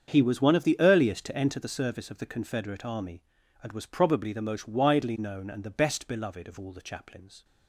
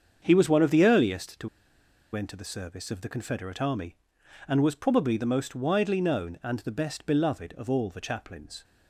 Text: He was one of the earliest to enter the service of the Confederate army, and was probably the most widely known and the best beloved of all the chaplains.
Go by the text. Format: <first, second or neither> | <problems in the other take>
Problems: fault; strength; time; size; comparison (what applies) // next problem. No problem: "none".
first | starts louder than the rest; strong; until 1.2 s; 7 dB; strong in the first // pauses between "to" and "enter"; noticeable; at 1.4 s; 0.66 s long